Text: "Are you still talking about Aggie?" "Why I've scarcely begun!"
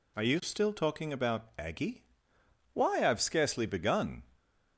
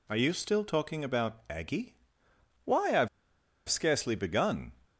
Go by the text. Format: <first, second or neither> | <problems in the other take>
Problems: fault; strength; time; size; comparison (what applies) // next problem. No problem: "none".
first | pauses between "I've" and "scarcely"; noticeable; at 3.0 s; 0.59 s long